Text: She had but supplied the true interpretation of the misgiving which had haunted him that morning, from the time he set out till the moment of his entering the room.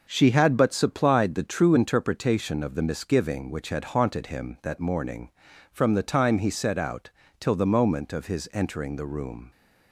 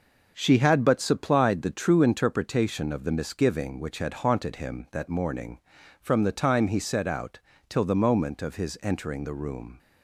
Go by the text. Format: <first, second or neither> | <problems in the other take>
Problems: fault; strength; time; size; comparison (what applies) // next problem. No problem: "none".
neither | starts louder than the rest; noticeable; the same in both // pauses between "out" and "till"; slight; the same in both